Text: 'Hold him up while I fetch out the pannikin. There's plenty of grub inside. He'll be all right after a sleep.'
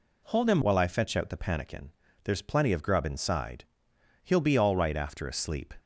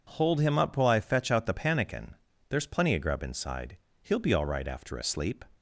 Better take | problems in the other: second | skips "up"; at 0.6 s

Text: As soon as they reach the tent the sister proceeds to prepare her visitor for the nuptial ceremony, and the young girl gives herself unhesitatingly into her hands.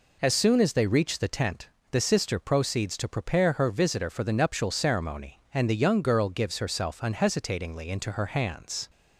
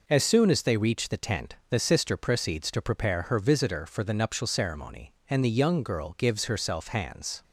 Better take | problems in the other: first | pauses between "tent" and "the"; slight; at 1.5 s; 0.16 s long; slight in the first // skips "unhesitatingly into her"; at 6.8 s

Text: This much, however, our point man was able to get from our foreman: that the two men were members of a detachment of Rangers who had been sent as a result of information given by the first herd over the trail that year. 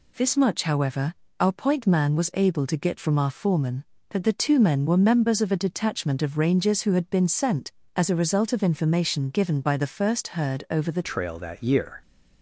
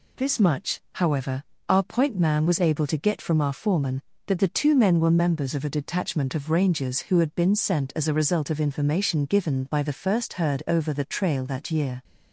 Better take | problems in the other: second | changes voice at "trail"; from 11.0 s on; 1.0 s long

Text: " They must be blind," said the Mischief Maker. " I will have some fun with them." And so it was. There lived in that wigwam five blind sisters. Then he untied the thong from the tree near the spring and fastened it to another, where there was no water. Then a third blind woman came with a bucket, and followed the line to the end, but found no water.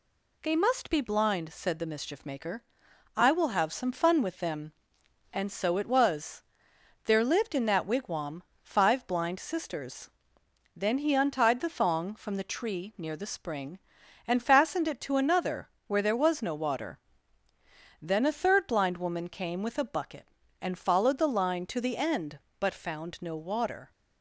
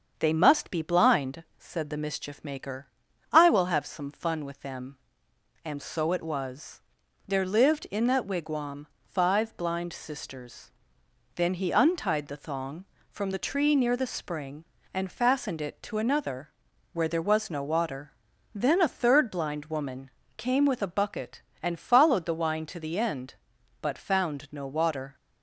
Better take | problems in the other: first | starts louder than the rest; until 1.1 s; 6.5 dB // pauses between "wigwam" and "five"; slight; at 8.8 s; 0.22 s long; slight in the first // pauses between "woman" and "came"; slight; at 20.1 s; 0.26 s long // says "wine" for "line"; at 22.3 s

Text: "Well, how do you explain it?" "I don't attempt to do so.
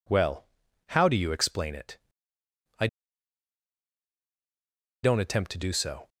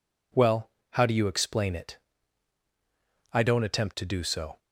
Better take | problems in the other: second | pauses between "I" and "don't"; strong; at 2.8 s; 2.1 s long

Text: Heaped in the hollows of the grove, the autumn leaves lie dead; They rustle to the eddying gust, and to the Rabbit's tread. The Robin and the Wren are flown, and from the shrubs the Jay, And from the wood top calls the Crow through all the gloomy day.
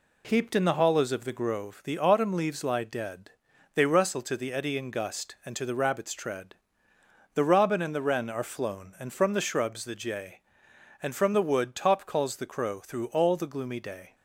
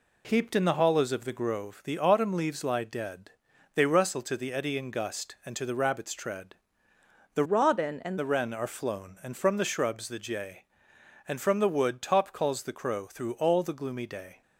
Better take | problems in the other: first | changes voice from "Robin" to "and"; from 7.4 to 8.1 s; 0.7 s long

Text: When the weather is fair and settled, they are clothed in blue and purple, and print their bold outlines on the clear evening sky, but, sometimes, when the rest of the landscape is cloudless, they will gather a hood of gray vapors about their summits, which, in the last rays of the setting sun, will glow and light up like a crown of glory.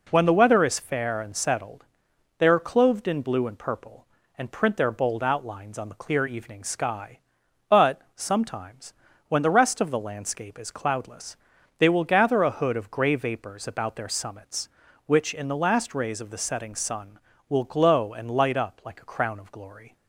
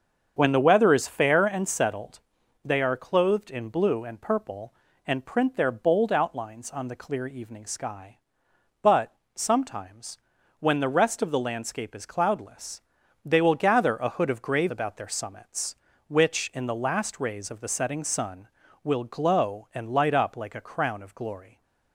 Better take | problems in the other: first | starts louder than the rest; until 1.3 s; 7 dB // skips "vapors"; at 14.6 s

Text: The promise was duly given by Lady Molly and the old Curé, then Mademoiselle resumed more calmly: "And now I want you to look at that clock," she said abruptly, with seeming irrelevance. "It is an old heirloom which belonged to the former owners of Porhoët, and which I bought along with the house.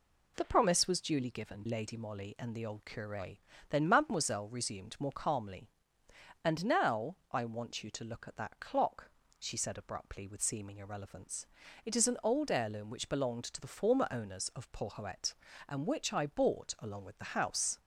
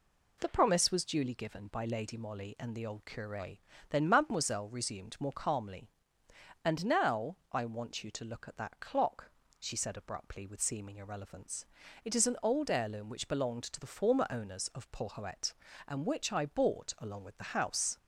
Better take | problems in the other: second | skips "by"; at 1.6 s // pauses between "now" and "I"; slight; at 7.1 s; 0.16 s long; slight in the second

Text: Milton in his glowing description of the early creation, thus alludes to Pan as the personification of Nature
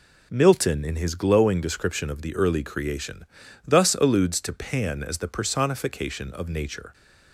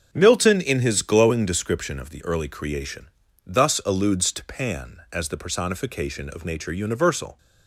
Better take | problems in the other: first | starts louder than the rest; until 1.1 s; 6.5 dB // goes on to say "Universal"; noticeable; from 6.7 s on; 0.64 s long

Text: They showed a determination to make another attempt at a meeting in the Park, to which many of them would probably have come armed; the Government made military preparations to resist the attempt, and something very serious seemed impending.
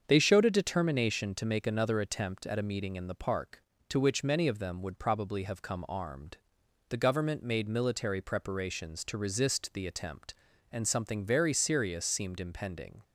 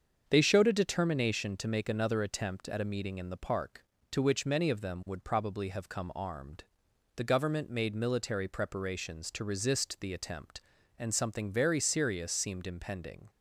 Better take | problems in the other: neither | starts louder than the rest; the same in both

